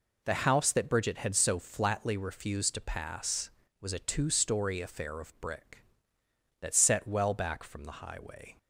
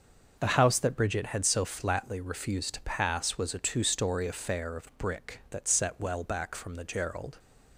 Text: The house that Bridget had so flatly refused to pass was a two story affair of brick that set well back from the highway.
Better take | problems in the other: first | starts louder than the rest; noticeable; until 1.3 s; 6 dB // says "gerald" for "highway"; at 6.8 s

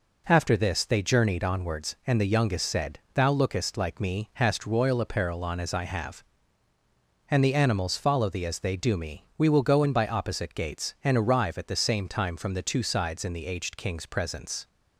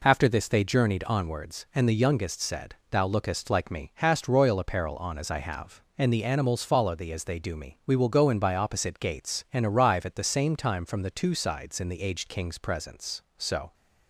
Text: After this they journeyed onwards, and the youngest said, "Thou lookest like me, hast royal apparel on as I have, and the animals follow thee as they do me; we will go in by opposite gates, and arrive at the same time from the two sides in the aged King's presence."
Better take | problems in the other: first | goes on to say "So"; slight; from 13.3 s on; 0.36 s long

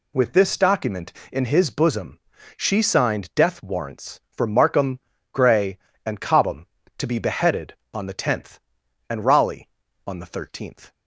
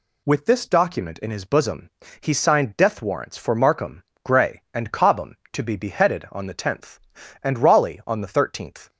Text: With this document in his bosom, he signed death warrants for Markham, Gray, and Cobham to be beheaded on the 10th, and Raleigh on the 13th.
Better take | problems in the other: second | says "she" for "he"; at 2.5 s

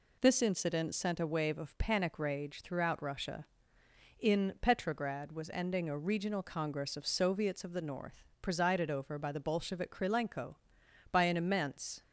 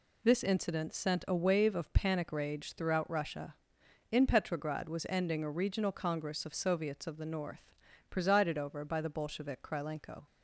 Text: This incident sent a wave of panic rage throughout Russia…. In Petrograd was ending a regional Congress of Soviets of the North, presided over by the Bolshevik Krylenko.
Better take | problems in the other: second | goes on to say "By an immense"; noticeable; from 11.1 s on; 0.90 s long

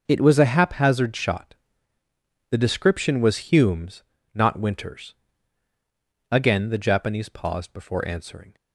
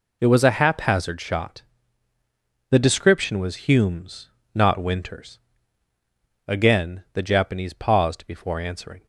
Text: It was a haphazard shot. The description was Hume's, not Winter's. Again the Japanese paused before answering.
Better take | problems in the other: neither | none

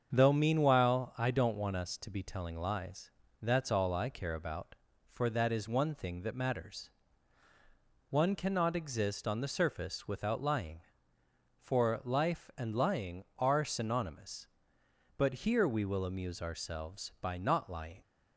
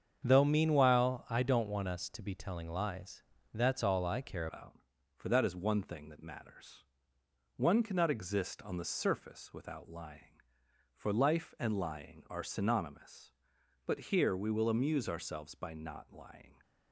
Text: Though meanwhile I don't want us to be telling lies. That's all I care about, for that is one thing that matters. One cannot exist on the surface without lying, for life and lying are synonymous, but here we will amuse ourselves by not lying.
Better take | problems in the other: first | starts louder than the rest; strong; until 1.2 s; 7.5 dB; also in the first // changes voice at "about"; from 4.4 s on; 12.1 s long

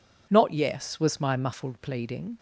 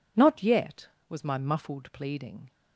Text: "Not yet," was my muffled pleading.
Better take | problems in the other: second | says "yes" for "yet"; at 0.5 s

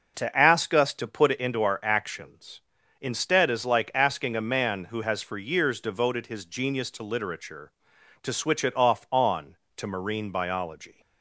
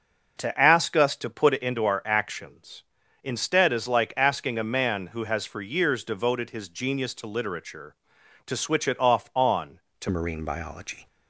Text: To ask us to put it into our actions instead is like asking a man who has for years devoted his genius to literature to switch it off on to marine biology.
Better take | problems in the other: first | changes voice at "marine"; from 10.1 s on; 0.9 s long

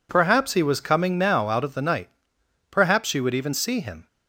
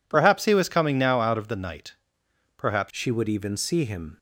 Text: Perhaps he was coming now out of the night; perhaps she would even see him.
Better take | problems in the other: first | changes voice at "she"; from 2.8 s on; 1.3 s long

